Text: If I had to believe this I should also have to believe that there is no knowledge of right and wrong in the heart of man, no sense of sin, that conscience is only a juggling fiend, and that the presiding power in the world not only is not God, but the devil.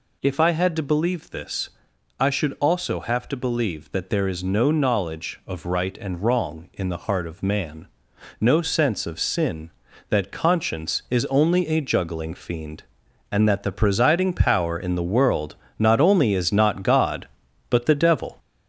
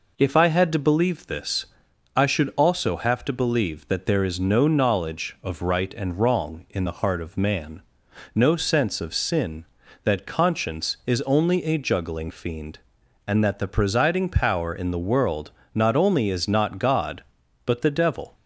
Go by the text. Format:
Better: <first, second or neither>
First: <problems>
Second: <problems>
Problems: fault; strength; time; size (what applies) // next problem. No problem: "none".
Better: second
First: gets louder; noticeable; throughout; 4 dB // pauses between "this" and "I"; noticeable; at 1.6 s; 0.50 s long // pauses between "world" and "not"; slight; at 15.5 s; 0.24 s long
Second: pauses between "this" and "I"; noticeable; at 1.6 s; 0.50 s long // pauses between "world" and "not"; slight; at 15.5 s; 0.24 s long